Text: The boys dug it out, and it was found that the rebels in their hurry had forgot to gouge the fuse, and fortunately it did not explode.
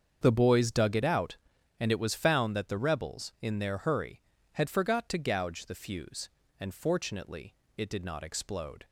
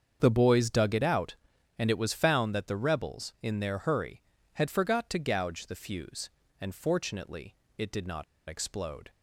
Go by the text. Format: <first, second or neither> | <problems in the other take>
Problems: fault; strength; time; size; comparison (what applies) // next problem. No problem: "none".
first | starts louder than the rest; strong; until 1.2 s; 7 dB; strong in the first // pauses between "fortunately" and "it"; slight; at 7.5 s; 0.24 s long; slight in the first // pauses between "not" and "explode"; slight; at 8.2 s; 0.25 s long